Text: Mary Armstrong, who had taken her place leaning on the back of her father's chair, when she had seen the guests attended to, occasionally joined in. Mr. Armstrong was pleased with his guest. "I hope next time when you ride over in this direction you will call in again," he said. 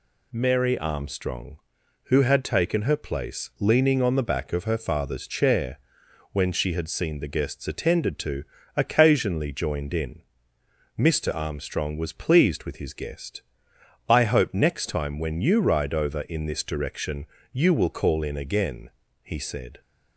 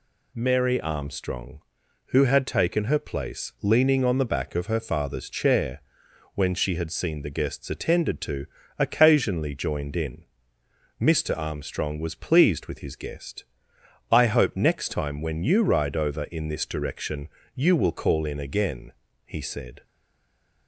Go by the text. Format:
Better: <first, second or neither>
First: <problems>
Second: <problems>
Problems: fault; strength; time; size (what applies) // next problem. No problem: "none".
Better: first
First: pauses between "direction" and "you"; slight; at 17.2 s; 0.26 s long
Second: pauses between "direction" and "you"; slight; at 17.2 s; 0.26 s long // stays silent after the last word; slight; from 19.8 s on; 0.8 s long